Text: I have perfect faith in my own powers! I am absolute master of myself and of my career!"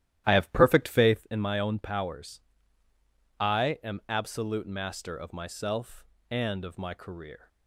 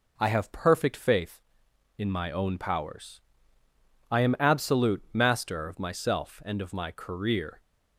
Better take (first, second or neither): second